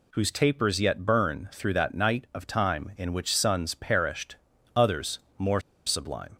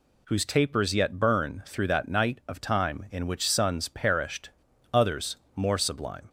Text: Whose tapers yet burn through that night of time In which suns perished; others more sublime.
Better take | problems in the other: second | pauses between "others" and "more"; slight; at 5.1 s; 0.18 s long; slight in the second // pauses between "more" and "sublime"; slight; at 5.5 s; 0.26 s long

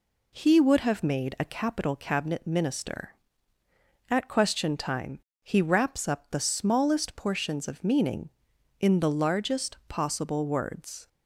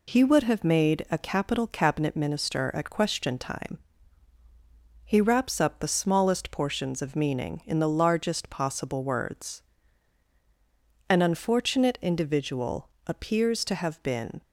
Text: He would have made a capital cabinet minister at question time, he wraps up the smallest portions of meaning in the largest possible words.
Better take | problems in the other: first | goes on to say "An unfortunate individual appears to have been"; strong; from 11.1 s on; 3.3 s long

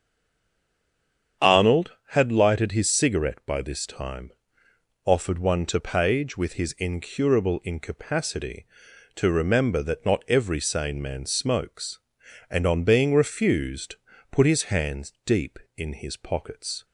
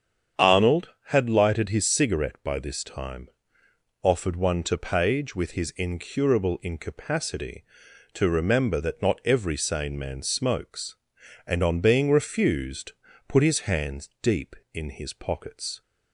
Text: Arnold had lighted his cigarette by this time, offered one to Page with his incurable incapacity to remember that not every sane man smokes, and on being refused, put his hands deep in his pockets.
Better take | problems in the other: second | stays silent before the first word; noticeable; until 1.4 s; 1.4 s long // starts louder than the rest; strong; until 2.5 s; 8 dB; strong in the second

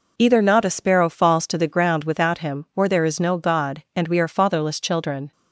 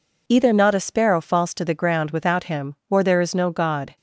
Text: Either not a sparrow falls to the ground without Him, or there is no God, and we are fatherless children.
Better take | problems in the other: first | stops before "and we are fatherless children"; at 3.9 s

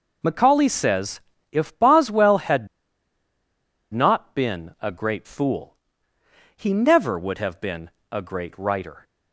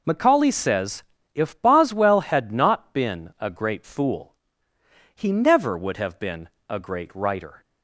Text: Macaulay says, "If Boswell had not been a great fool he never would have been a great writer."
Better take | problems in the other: second | pauses between "had" and "not"; strong; at 2.6 s; 1.2 s long // pauses between "fool" and "he"; noticeable; at 5.7 s; 0.80 s long; noticeable in the second // pauses between "been" and "a"; slight; at 7.8 s; 0.20 s long; slight in the second

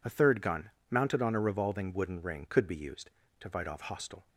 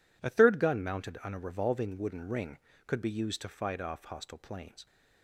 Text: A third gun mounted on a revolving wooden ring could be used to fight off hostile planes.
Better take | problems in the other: second | pauses between "gun" and "mounted"; slight; at 0.6 s; 0.22 s long // stops before "planes"; at 4.2 s

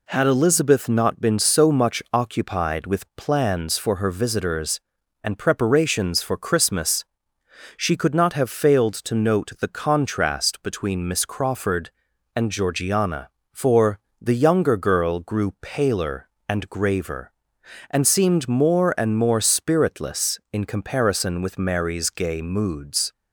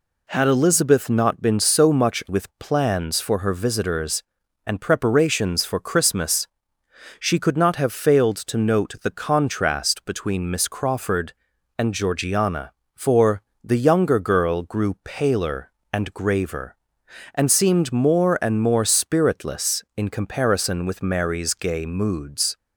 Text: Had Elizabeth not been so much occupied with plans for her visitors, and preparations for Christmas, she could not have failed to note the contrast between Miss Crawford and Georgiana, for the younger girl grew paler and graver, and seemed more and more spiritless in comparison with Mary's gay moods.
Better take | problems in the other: first | skips "occupied"; at 2.2 s // pauses between "for" and "the"; slight; at 13.4 s; 0.22 s long; slight in the first

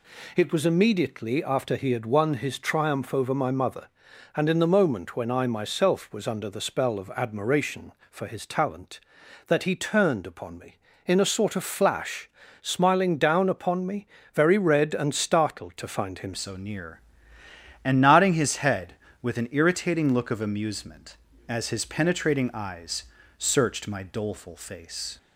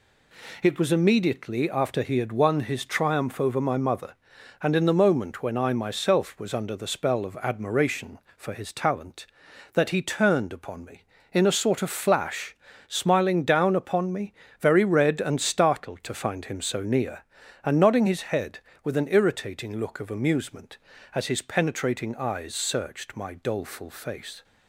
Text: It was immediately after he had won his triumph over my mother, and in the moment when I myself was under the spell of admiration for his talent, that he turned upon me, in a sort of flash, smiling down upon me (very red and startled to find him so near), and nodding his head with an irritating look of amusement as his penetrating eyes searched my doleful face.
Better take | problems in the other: second | changes voice at "so"; from 16.3 s on; 8.8 s long // pauses between "eyes" and "searched"; slight; at 23.0 s; 0.34 s long

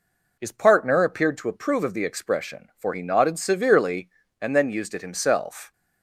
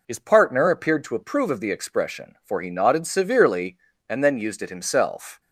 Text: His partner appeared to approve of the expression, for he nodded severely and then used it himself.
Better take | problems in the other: neither | none

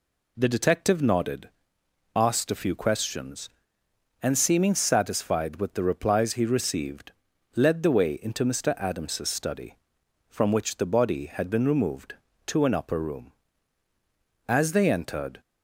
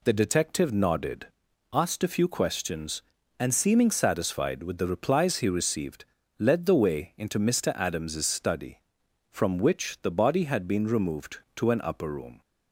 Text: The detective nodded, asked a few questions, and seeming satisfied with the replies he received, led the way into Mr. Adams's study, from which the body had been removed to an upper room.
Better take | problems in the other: second | goes on to say "As they entered"; noticeable; from 14.4 s on; 0.92 s long

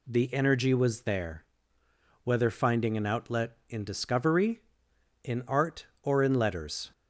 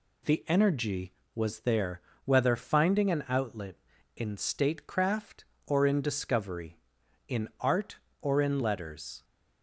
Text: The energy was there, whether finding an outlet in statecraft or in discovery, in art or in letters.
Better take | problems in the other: second | skips "statecraft or in"; at 3.8 s

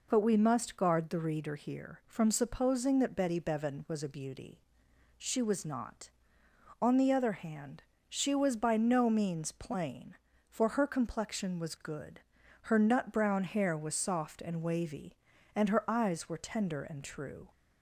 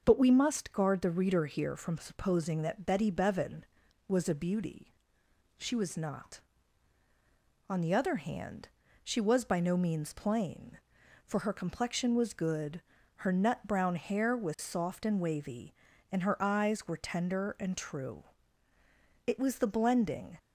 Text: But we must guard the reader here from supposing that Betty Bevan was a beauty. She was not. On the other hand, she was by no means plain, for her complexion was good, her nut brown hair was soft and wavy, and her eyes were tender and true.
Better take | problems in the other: first | starts louder than the rest; until 1.0 s; 6.5 dB // goes on to say "It was the blending"; noticeable; from 19.2 s on; 1.1 s long

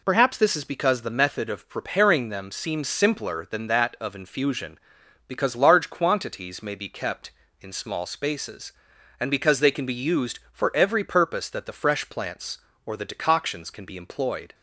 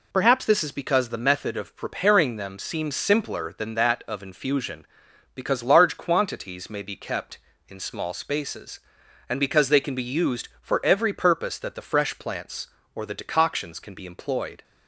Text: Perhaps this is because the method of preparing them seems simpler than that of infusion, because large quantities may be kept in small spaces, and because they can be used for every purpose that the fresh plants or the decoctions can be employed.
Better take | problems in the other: neither | none

